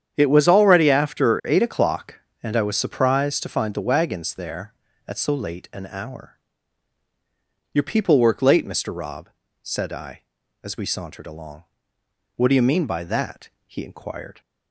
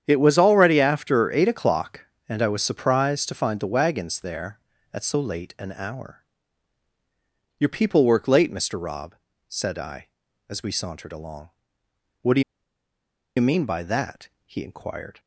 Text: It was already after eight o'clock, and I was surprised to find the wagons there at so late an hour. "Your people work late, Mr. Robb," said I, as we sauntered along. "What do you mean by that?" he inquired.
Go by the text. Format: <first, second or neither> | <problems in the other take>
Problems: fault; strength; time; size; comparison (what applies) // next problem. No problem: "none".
first | starts louder than the rest; strong; until 1.0 s; 8.5 dB; strong in the first // pauses between "do" and "you"; noticeable; at 12.4 s; 0.96 s long